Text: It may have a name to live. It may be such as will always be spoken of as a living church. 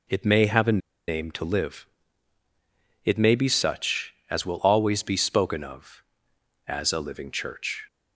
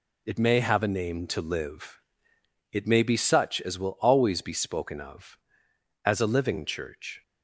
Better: second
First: pauses between "a" and "name"; slight; at 0.7 s; 0.28 s long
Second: none

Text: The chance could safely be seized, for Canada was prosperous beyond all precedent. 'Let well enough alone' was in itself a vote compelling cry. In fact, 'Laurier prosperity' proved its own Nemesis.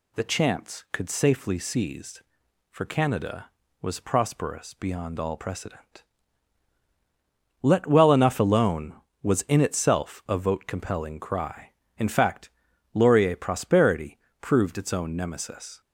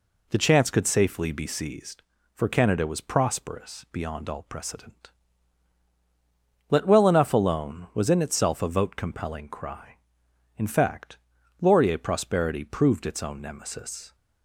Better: second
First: skips "be"; at 1.5 s // pauses between "prosperity" and "proved"; slight; at 14.1 s; 0.22 s long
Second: none

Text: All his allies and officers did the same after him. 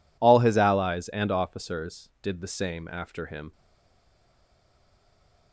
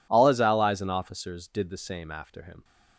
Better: second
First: stays silent after the last word; noticeable; from 3.5 s on; 2.0 s long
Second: none

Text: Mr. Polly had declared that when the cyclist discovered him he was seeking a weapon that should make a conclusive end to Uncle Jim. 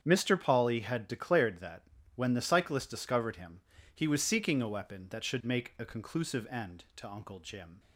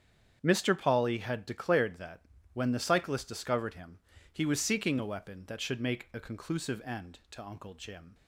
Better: neither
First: starts louder than the rest; strong; until 1.0 s; 8 dB // pauses between "that" and "when"; slight; at 1.8 s; 0.32 s long // pauses between "him" and "he"; slight; at 3.6 s; 0.32 s long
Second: starts louder than the rest; strong; until 1.4 s; 8 dB // pauses between "that" and "when"; slight; at 2.2 s; 0.32 s long // pauses between "him" and "he"; slight; at 3.9 s; 0.32 s long

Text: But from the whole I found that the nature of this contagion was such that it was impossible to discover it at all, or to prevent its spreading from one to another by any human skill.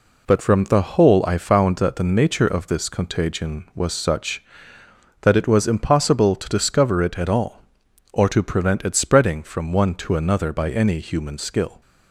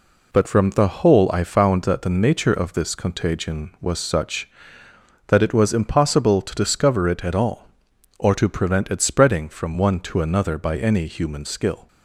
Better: neither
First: none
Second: none

